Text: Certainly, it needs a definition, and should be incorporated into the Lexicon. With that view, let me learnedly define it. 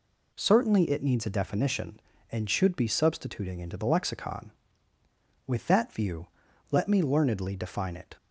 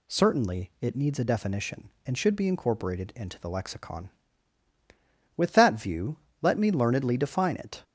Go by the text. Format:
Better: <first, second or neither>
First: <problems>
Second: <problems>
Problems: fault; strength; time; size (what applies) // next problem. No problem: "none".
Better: second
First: says "substituting" for "incorporated"; at 2.8 s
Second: none